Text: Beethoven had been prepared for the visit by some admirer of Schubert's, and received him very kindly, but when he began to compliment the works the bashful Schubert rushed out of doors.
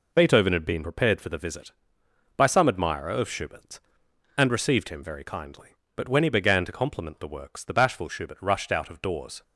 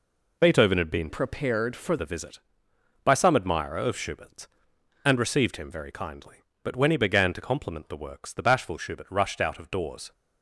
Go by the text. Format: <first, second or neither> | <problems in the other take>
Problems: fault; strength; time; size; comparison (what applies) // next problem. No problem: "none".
first | changes voice from "prepared" to "for"; from 1.0 to 1.9 s; 0.9 s long